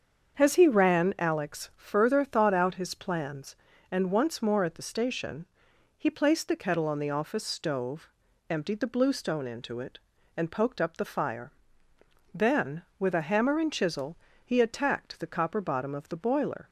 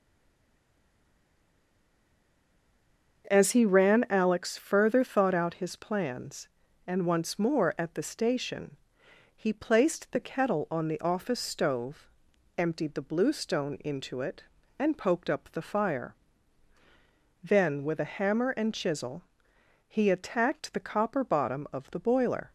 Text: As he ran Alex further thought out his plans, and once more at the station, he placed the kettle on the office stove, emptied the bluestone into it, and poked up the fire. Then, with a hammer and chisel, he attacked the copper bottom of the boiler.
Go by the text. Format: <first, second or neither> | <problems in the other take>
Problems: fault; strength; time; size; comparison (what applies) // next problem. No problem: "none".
first | stays silent before the first word; strong; until 3.2 s; 3.2 s long // starts louder than the rest; until 4.3 s; 6.5 dB; also in the first